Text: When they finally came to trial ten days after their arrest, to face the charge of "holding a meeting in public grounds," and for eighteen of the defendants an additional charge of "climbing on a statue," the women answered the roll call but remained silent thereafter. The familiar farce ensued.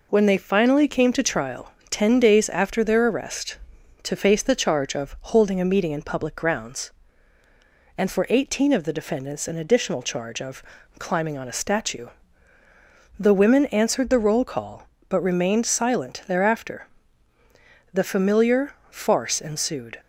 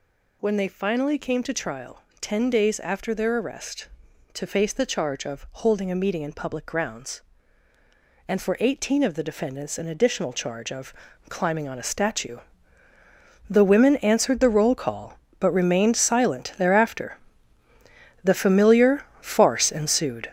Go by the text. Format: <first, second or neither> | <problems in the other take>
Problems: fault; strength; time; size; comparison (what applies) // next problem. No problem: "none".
first | gets louder; strong; throughout; 7.5 dB // pauses between "trial" and "ten"; slight; at 2.0 s; 0.22 s long; slight in the first // pauses between "of" and "climbing"; slight; at 10.9 s; 0.34 s long; slight in the first // pauses between "familiar" and "farce"; slight; at 19.0 s; 0.16 s long; slight in the first